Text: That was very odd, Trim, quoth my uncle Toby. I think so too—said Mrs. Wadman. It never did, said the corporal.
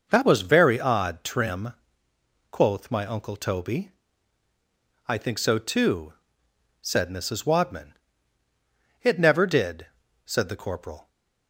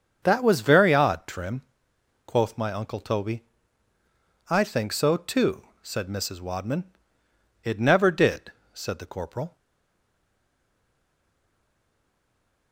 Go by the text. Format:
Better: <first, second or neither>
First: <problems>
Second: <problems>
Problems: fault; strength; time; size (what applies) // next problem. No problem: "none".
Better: first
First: none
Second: starts louder than the rest; until 1.2 s; 7 dB // stays silent after the last word; strong; from 9.5 s on; 3.2 s long